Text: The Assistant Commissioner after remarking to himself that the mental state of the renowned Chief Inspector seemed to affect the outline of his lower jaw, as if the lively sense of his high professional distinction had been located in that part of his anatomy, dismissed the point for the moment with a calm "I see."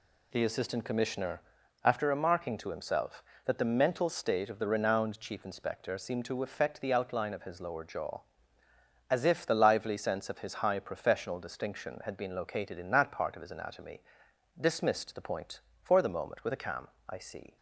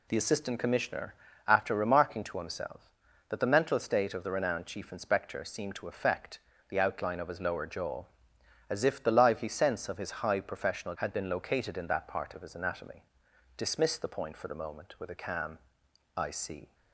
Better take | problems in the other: first | pauses between "Commissioner" and "after"; slight; at 1.1 s; 0.34 s long; also in the first // pauses between "affect" and "the"; slight; at 6.3 s; 0.30 s long // skips "distinction"; at 10.9 s // pauses between "calm" and "I"; noticeable; at 15.5 s; 0.58 s long; slight in the first

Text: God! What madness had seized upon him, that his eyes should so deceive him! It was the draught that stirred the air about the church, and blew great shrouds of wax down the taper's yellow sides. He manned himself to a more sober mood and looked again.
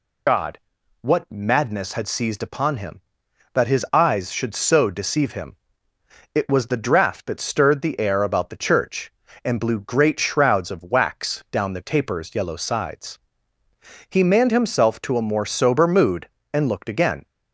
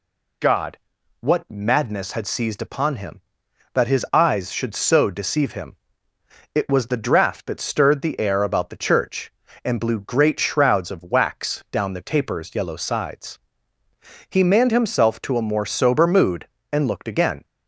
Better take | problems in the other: second | loses the start of "God"; at 0.2 s; 65 ms

